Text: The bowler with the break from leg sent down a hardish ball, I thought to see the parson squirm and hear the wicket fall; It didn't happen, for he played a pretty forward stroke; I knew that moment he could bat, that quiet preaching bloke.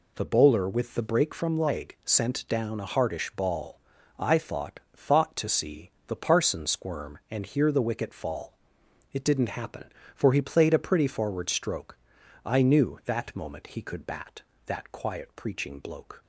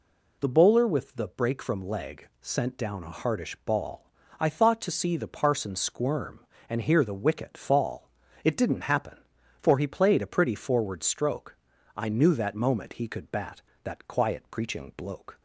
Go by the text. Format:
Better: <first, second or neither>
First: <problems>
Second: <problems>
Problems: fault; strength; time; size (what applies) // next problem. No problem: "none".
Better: second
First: says "thought" twice; at 4.9 s // pauses between "see" and "the"; slight; at 5.8 s; 0.16 s long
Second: none